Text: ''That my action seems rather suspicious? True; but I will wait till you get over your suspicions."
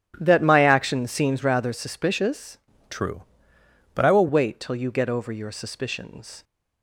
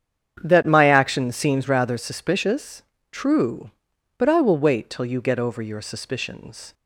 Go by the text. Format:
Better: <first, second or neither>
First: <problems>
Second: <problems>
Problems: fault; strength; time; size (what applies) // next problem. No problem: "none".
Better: second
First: starts louder than the rest; strong; until 1.2 s; 11 dB // changes voice from "True" to "will"; from 2.8 to 4.2 s; 1.4 s long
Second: starts louder than the rest; strong; until 1.4 s; 8.5 dB